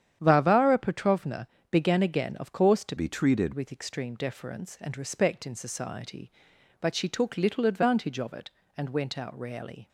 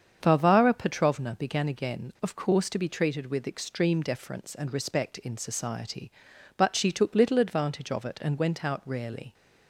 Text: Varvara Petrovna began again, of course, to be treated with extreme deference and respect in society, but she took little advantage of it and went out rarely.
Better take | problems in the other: second | starts louder than the rest; strong; until 1.2 s; 9.5 dB; strong in the second // pauses between "Petrovna" and "began"; slight; at 1.4 s; 0.26 s long // changes voice from "be" to "treated"; from 2.9 to 3.5 s; 0.6 s long

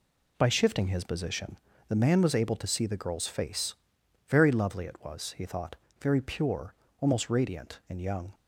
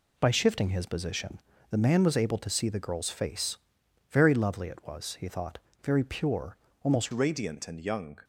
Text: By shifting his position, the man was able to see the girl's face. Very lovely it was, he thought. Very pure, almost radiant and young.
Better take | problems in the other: first | changes voice at "radiant"; from 7.1 s on; 1.1 s long

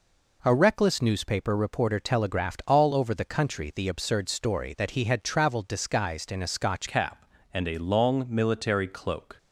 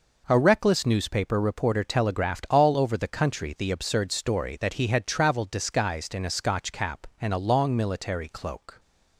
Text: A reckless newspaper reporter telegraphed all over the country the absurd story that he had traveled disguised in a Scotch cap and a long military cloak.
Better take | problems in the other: second | changes voice at "cap"; from 6.8 s on; 2.5 s long

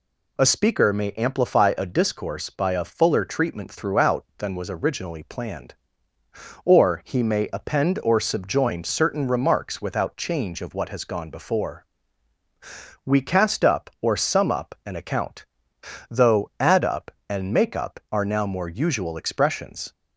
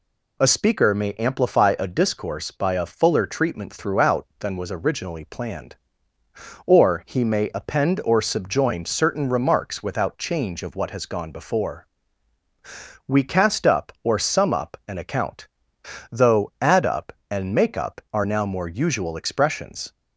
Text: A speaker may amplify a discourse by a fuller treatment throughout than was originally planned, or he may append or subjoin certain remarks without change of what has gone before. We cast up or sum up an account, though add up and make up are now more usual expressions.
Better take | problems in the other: neither | none

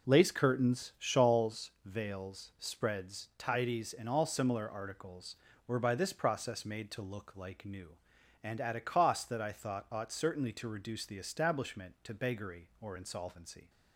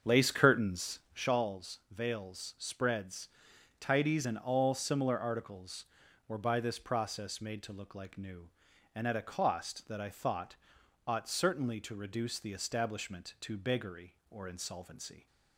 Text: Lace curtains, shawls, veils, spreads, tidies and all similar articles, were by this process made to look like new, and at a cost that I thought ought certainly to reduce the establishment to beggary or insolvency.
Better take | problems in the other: first | starts louder than the rest; until 1.3 s; 7 dB // pauses between "thought" and "ought"; noticeable; at 10.5 s; 0.50 s long

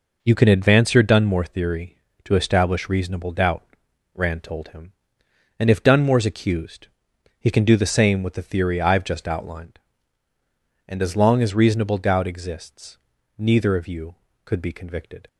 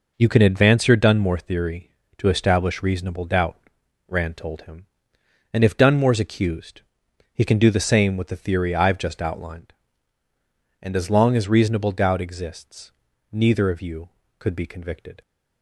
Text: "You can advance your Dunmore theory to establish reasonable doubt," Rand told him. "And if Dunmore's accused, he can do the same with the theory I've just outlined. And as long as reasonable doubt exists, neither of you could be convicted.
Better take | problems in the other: neither | none

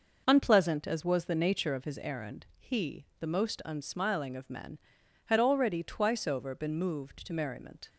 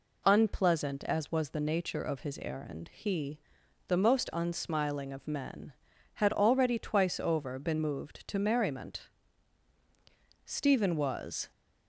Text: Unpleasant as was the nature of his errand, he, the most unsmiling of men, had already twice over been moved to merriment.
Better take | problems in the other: first | goes on to say "Stephen was"; noticeable; from 10.4 s on; 1.0 s long

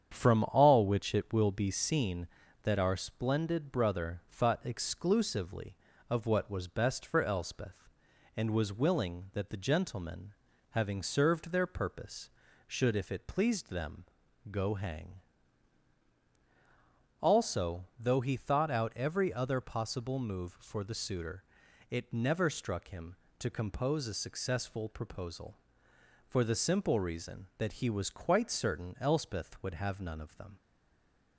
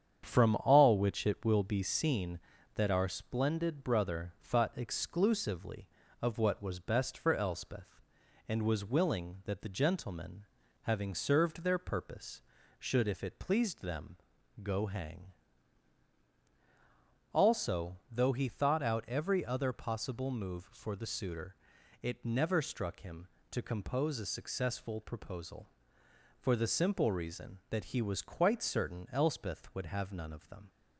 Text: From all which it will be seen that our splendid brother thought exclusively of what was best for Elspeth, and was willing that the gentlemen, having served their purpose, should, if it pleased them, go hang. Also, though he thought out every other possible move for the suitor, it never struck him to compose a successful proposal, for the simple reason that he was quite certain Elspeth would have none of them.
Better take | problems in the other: second | starts louder than the rest; strong; until 1.1 s; 8.5 dB; strong in the second // stays silent after the last word; slight; from 30.5 s on; 0.8 s long

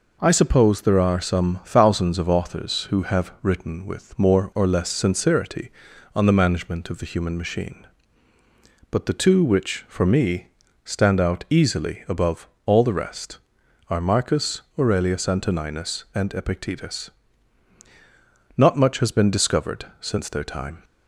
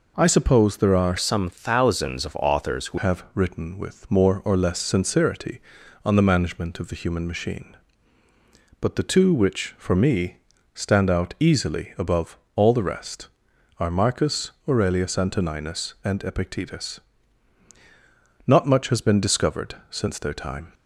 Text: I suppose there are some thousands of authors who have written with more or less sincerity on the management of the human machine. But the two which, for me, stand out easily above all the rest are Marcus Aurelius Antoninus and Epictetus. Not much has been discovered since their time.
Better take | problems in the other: first | changes voice from "some" to "who"; from 1.1 to 2.9 s; 1.8 s long // pauses between "above" and "all"; slight; at 12.3 s; 0.18 s long; slight in the first // pauses between "Marcus" and "Aurelius"; slight; at 14.5 s; 0.16 s long; slight in the first

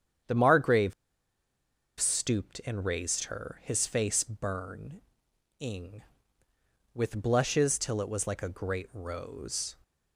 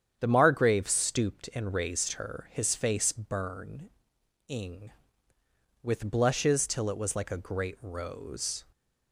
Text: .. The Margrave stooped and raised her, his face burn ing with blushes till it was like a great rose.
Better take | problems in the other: second | starts louder than the rest; strong; until 2.3 s; 8.5 dB; strong in the second // pauses between "Margrave" and "stooped"; at 0.9 s; 1.0 s long // pauses between "burn" and "ing"; noticeable; at 5.0 s; 0.56 s long; noticeable in the second

